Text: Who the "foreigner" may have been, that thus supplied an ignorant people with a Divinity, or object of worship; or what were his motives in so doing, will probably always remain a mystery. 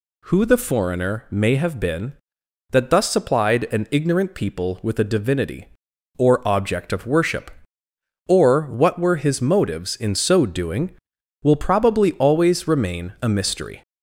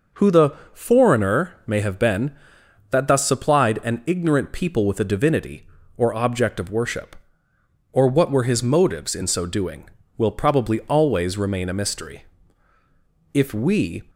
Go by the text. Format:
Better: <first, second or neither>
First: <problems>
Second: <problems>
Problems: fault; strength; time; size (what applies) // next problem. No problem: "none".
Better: first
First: none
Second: pauses between "the" and "foreigner"; slight; at 0.5 s; 0.20 s long // goes on to say "If we"; noticeable; from 13.3 s on; 0.70 s long